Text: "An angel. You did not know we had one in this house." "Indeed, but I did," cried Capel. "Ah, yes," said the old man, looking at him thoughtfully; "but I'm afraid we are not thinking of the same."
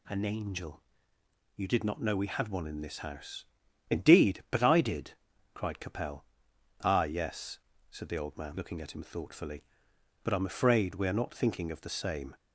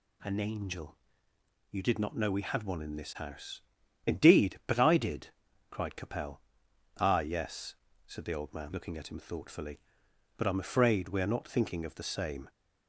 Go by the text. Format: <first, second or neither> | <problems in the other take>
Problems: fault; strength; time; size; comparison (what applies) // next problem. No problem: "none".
neither | none